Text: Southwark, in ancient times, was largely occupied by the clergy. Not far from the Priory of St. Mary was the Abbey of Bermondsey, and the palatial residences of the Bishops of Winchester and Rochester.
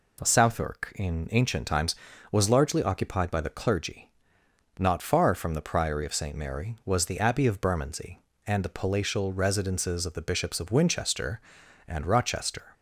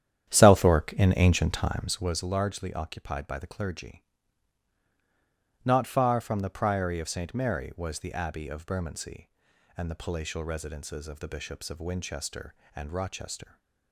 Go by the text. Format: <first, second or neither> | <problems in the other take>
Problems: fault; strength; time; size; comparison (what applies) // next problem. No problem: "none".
first | starts louder than the rest; strong; until 2.2 s; 10 dB